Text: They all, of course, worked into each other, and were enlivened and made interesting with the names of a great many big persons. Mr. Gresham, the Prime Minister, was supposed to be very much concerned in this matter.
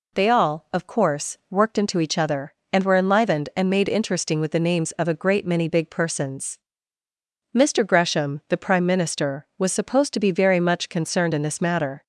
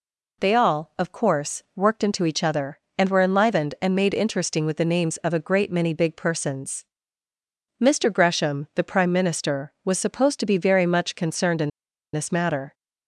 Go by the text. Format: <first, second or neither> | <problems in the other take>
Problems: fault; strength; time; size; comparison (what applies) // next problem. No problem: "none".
first | pauses between "in" and "this"; at 11.7 s; 0.43 s long